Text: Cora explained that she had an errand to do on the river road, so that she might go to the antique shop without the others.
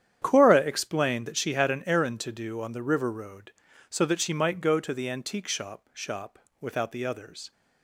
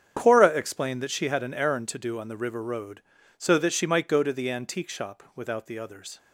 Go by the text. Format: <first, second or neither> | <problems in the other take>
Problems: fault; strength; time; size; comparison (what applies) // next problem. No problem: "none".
second | starts louder than the rest; strong; until 1.2 s; 9.5 dB; strong in the second // says "shop" twice; at 5.9 s